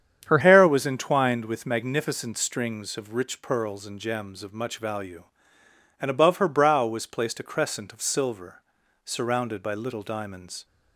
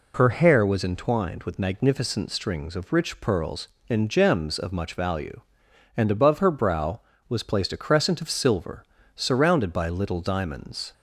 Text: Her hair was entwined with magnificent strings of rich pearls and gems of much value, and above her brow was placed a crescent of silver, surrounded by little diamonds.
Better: second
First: starts louder than the rest; strong; until 1.3 s; 8.5 dB // changes voice at "hair"; from 0.3 s on; 10.3 s long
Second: none

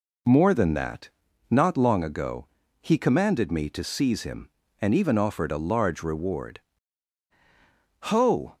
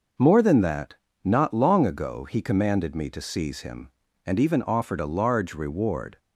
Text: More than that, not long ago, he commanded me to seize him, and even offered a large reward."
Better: second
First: goes on to say "Ho"; from 8.0 s on; 0.56 s long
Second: none

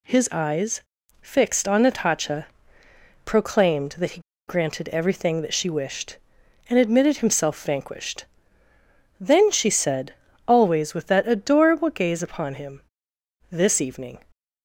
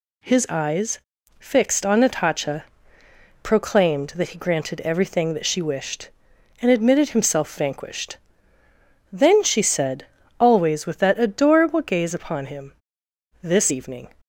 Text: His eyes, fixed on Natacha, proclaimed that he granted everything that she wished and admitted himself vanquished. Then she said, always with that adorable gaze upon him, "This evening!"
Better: second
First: pauses between "he" and "granted"; slight; at 4.1 s; 0.28 s long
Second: none

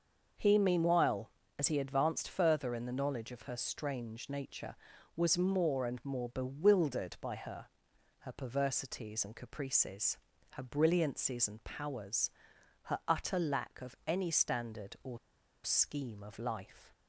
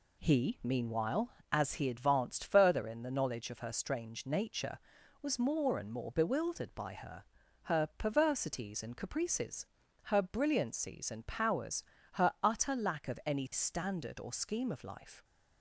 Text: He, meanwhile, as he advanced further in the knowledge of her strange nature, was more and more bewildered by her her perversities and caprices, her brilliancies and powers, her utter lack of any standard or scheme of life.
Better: second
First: starts louder than the rest; until 1.6 s; 6 dB // pauses between "her" and "her"; noticeable; at 7.6 s; 0.52 s long // pauses between "or" and "scheme"; noticeable; at 15.1 s; 0.47 s long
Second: pauses between "her" and "her"; at 7.2 s; 0.40 s long

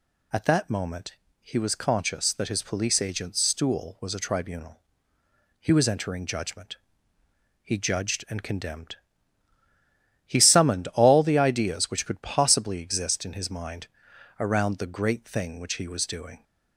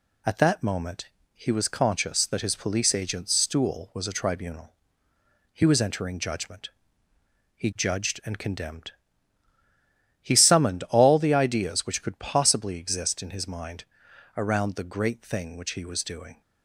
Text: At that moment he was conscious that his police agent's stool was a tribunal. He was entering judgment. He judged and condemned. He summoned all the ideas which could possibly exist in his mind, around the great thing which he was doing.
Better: first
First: pauses between "moment" and "he"; slight; at 1.1 s; 0.26 s long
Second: gets quieter; slight; throughout; 2.5 dB // pauses between "moment" and "he"; slight; at 1.0 s; 0.26 s long

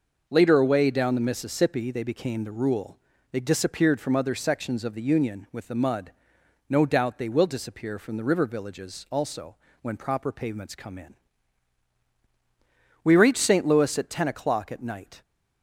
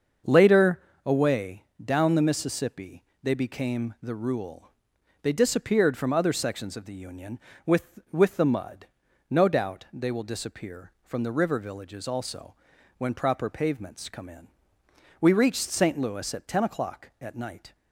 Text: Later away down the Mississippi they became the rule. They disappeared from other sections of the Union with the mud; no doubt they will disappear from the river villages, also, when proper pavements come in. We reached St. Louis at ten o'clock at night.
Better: first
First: none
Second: starts louder than the rest; until 1.4 s; 6.5 dB // pauses between "Later" and "away"; slight; at 0.8 s; 0.24 s long // pauses between "away" and "down"; slight; at 1.6 s; 0.18 s long // pauses between "Mississippi" and "they"; slight; at 3.0 s; 0.20 s long // says "with" twice; at 8.1 s

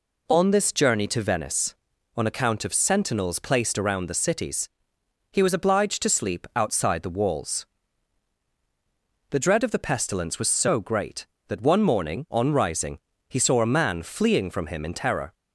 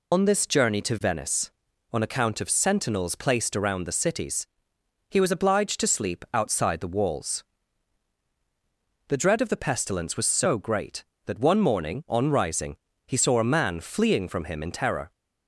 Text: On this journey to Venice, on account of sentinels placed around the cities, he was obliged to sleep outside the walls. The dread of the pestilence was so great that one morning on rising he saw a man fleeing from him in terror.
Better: first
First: pauses between "rising" and "he"; slight; at 12.9 s; 0.30 s long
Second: loses the start of "On"; at 0.1 s; 100 ms // pauses between "rising" and "he"; slight; at 12.7 s; 0.30 s long

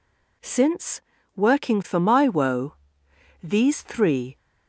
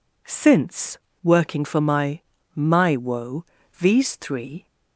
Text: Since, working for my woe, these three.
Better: first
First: none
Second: says "my" twice; at 2.5 s

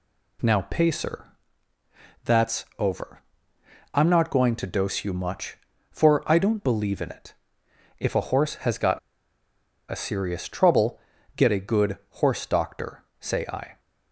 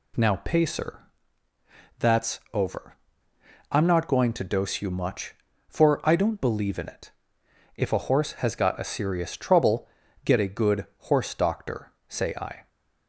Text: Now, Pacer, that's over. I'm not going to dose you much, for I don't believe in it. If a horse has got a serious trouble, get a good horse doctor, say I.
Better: second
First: pauses between "got" and "a"; noticeable; at 8.9 s; 0.91 s long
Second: none

